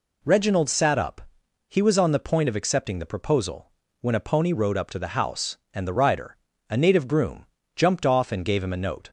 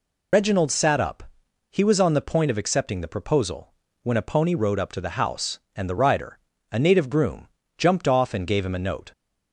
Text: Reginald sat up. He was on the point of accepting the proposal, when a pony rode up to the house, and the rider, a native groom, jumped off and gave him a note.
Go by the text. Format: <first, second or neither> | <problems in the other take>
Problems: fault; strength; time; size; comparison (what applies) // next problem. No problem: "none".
first | loses the start of "Reginald"; at 0.3 s; 75 ms